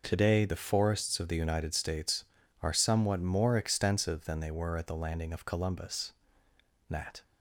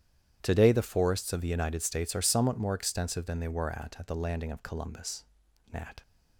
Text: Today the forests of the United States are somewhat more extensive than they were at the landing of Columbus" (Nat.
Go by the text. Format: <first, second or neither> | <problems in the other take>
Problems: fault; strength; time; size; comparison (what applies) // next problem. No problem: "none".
first | starts louder than the rest; strong; until 1.4 s; 10.5 dB // says "at" twice; at 3.9 s